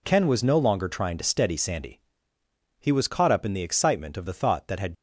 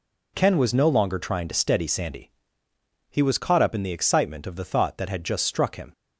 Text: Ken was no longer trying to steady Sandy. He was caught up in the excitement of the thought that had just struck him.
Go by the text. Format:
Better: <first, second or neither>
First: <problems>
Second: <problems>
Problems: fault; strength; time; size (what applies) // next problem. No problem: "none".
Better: second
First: stops before "just struck him"; at 4.9 s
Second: none